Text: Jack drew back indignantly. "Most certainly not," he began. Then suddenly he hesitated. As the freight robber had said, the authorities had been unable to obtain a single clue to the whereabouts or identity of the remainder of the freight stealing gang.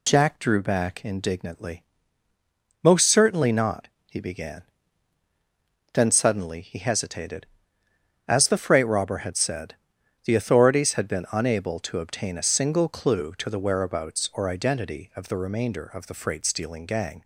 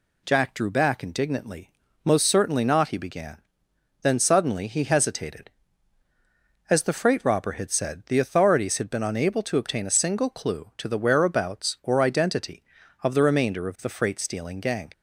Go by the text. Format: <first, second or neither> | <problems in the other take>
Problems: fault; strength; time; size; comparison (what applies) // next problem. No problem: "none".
neither | none